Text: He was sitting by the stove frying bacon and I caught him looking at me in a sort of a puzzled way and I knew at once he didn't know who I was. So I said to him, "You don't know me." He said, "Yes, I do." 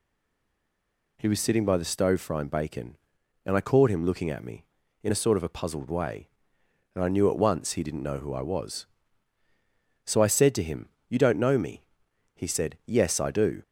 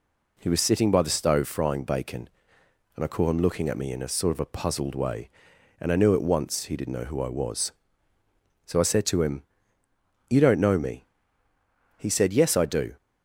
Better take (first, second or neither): second